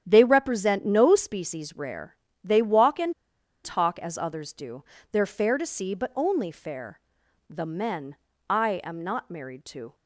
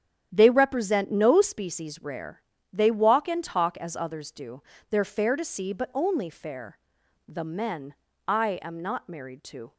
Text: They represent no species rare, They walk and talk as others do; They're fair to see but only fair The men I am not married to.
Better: second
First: starts louder than the rest; strong; until 1.0 s; 9.5 dB // pauses between "and" and "talk"; noticeable; at 3.1 s; 0.51 s long // pauses between "fair" and "The"; noticeable; at 7.0 s; 0.50 s long // pauses between "men" and "I"; slight; at 8.1 s; 0.34 s long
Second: starts louder than the rest; strong; until 1.3 s; 9.5 dB // pauses between "fair" and "The"; noticeable; at 6.7 s; 0.50 s long // pauses between "men" and "I"; slight; at 7.9 s; 0.34 s long

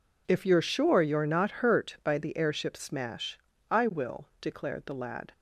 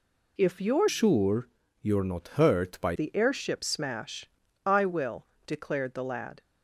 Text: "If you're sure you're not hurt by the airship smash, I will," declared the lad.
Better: first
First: none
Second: changes voice from "sure" to "by"; from 0.8 to 2.9 s; 2.1 s long // pauses between "sure" and "you're"; slight; at 1.4 s; 0.34 s long

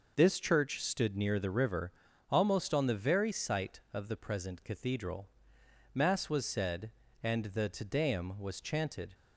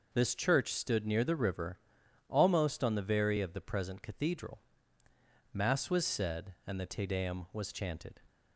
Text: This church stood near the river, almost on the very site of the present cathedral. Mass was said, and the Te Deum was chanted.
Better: first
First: none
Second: skips "site"; at 3.3 s

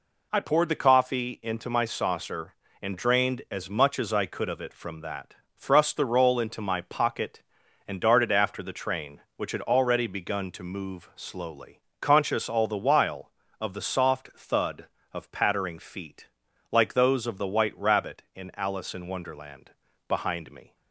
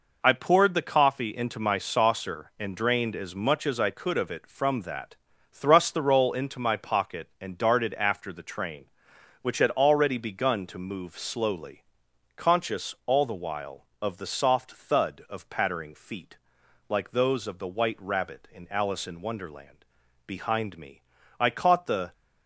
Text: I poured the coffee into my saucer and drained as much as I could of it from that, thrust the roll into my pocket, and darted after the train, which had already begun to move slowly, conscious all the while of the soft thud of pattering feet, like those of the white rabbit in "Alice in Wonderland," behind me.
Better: first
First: none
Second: goes on to say "I caught the"; noticeable; from 21.3 s on; 0.74 s long

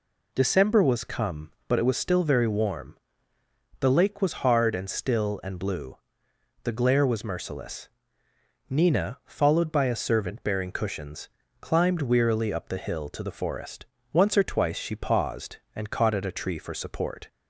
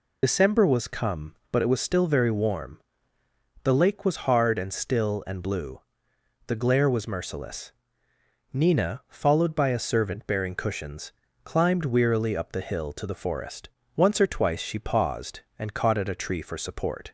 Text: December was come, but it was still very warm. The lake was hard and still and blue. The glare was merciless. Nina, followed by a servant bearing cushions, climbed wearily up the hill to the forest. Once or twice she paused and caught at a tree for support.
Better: first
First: none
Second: loses the start of "December"; at 0.2 s; 60 ms

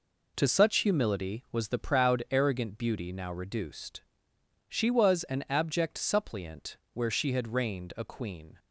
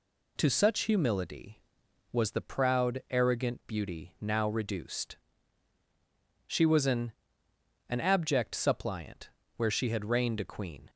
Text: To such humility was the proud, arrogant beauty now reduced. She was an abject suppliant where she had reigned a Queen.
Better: first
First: pauses between "suppliant" and "where"; slight; at 6.7 s; 0.16 s long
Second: says "an" twice; at 7.8 s // pauses between "suppliant" and "where"; slight; at 9.2 s; 0.26 s long

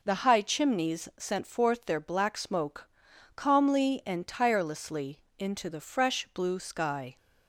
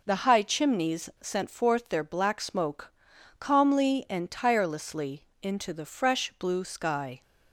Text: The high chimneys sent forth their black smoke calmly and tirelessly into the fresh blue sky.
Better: neither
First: pauses between "smoke" and "calmly"; noticeable; at 2.8 s; 0.46 s long // pauses between "tirelessly" and "into"; slight; at 5.2 s; 0.16 s long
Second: pauses between "smoke" and "calmly"; noticeable; at 2.9 s; 0.46 s long // pauses between "tirelessly" and "into"; slight; at 5.2 s; 0.16 s long

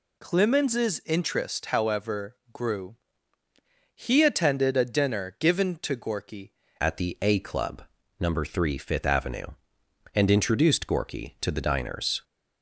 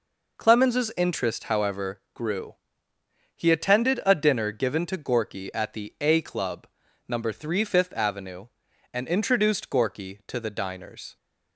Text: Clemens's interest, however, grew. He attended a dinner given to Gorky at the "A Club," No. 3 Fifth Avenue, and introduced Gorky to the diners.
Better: second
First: changes voice at "at"; from 6.7 s on; 5.5 s long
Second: none

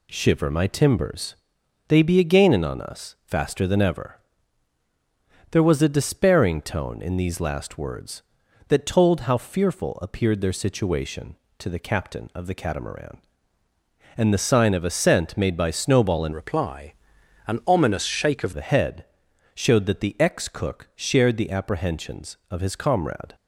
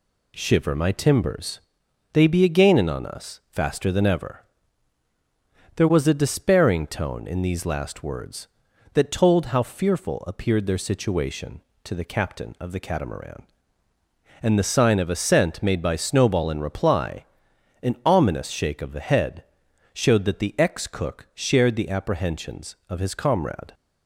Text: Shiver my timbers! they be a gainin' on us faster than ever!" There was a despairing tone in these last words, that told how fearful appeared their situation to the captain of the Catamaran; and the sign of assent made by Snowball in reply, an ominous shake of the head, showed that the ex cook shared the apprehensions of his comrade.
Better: second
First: changes voice from "reply" to "of"; from 16.3 to 18.5 s; 2.2 s long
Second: none

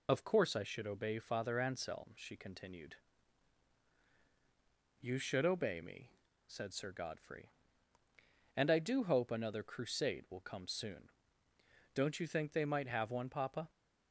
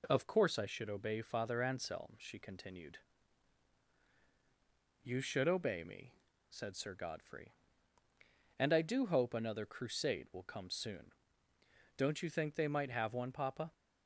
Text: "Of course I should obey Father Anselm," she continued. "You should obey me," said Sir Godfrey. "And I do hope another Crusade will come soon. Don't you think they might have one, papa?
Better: second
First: loses the start of "Of"; at 0.0 s; 80 ms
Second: none

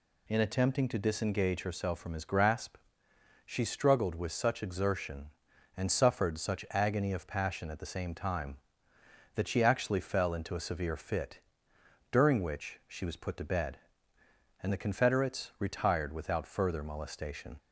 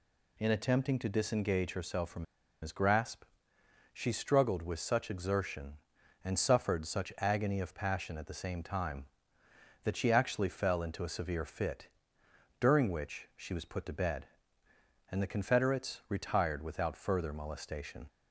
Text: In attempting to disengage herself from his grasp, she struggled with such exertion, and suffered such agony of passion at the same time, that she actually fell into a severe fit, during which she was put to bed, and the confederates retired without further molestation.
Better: first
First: none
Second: pauses between "from" and "his"; at 2.2 s; 0.37 s long

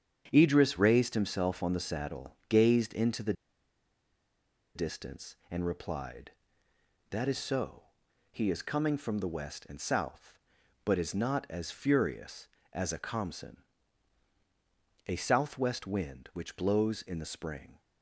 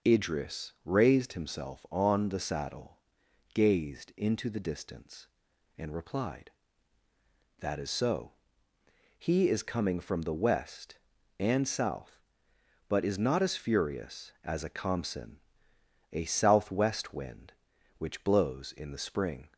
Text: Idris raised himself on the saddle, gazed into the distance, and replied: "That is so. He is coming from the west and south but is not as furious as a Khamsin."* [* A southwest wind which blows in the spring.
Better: second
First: starts louder than the rest; strong; until 1.3 s; 8 dB // pauses between "the" and "distance"; strong; at 3.3 s; 1.4 s long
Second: starts louder than the rest; noticeable; until 1.1 s; 6 dB

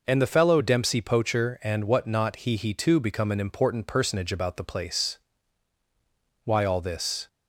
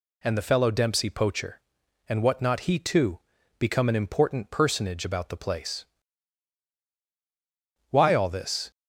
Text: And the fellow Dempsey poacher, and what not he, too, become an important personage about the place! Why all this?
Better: second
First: says "he" twice; at 2.5 s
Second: none

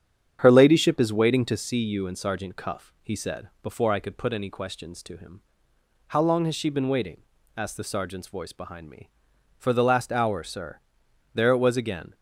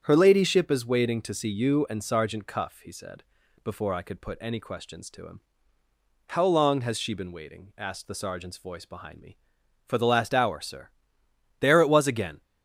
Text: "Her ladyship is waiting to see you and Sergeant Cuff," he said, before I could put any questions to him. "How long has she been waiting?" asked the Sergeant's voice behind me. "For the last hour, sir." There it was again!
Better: neither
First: starts louder than the rest; strong; until 1.4 s; 9 dB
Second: starts louder than the rest; strong; until 1.0 s; 8 dB

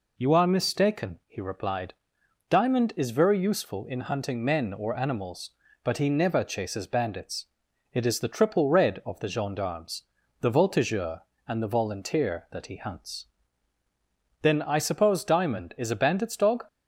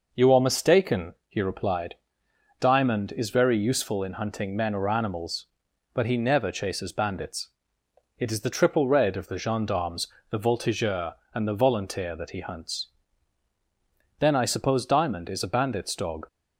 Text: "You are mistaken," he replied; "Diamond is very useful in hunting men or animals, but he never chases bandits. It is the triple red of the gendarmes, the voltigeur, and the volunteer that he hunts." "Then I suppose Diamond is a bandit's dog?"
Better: neither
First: none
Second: none

